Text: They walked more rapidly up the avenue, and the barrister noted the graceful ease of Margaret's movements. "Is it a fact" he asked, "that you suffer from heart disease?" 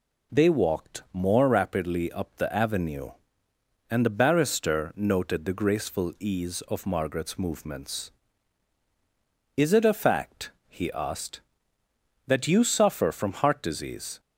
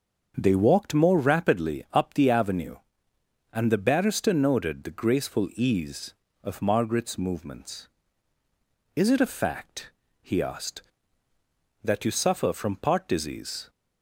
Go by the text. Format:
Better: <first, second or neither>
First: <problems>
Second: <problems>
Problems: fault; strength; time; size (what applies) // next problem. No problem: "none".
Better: first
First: pauses between "fact" and "he"; slight; at 10.4 s; 0.18 s long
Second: starts louder than the rest; until 1.3 s; 6.5 dB // pauses between "fact" and "he"; slight; at 9.9 s; 0.30 s long // says "part" for "heart"; at 12.7 s